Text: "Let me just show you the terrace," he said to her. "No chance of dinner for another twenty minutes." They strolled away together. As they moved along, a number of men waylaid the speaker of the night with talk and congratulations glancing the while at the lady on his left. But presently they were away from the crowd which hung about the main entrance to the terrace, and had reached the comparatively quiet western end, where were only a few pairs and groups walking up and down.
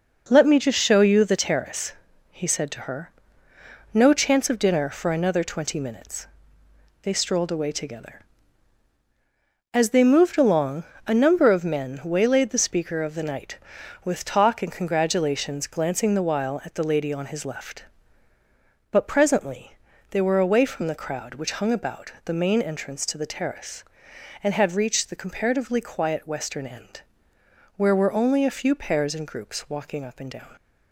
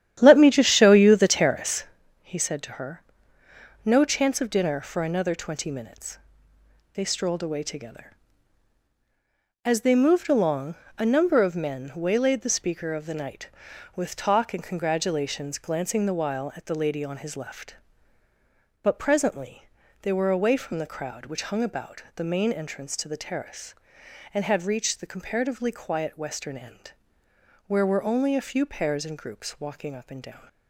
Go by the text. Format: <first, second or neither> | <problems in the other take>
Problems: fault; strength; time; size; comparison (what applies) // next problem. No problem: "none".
first | starts louder than the rest; strong; until 2.0 s; 11 dB // pauses between "presently" and "they"; slight; at 19.6 s; 0.34 s long; slight in the first